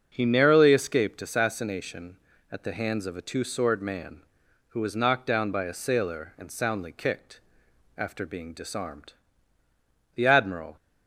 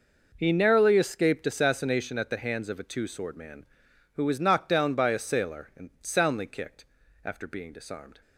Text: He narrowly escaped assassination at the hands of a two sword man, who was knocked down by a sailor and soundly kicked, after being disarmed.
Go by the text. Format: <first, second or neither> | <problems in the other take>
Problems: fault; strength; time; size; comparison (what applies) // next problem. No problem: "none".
second | starts louder than the rest; until 1.1 s; 6.5 dB // goes on to say "The Admiral"; from 10.1 s on; 0.60 s long